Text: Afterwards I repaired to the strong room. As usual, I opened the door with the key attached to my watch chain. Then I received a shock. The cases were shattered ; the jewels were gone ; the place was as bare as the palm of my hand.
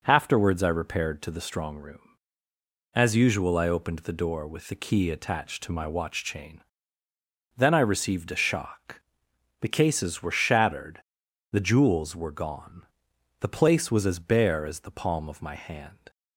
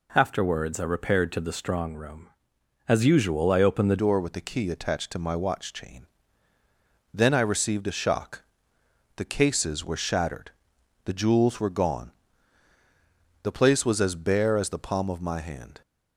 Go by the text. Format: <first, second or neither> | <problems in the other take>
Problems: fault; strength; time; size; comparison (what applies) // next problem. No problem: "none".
first | changes voice at "door"; from 3.9 s on; 11.9 s long